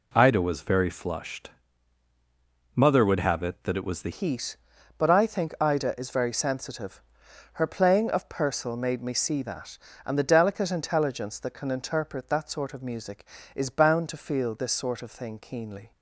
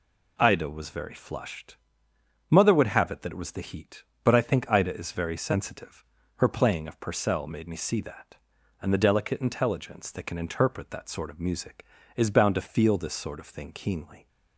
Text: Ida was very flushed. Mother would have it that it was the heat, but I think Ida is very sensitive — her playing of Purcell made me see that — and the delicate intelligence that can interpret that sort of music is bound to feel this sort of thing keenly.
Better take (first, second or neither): second